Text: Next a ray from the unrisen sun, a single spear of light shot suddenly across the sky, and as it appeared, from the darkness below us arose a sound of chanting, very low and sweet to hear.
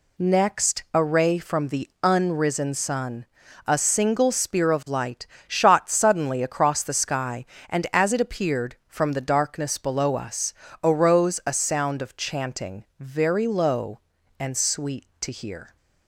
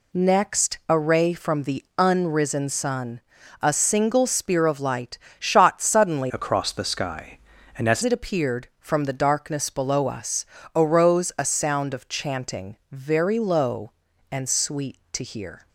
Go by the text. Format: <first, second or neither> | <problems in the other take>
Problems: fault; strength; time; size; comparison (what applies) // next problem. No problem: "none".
first | pauses between "light" and "shot"; slight; at 5.1 s; 0.20 s long; slight in the first // changes voice from "across" to "as"; from 6.3 to 8.0 s; 1.7 s long // pauses between "us" and "arose"; slight; at 10.4 s; 0.28 s long; slight in the first